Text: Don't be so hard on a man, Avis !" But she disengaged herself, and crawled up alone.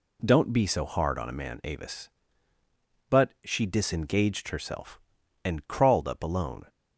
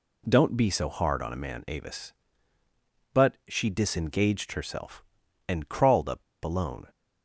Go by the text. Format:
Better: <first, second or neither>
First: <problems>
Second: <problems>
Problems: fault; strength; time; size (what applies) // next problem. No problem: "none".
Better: first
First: none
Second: pauses between "up" and "alone"; slight; at 6.2 s; 0.22 s long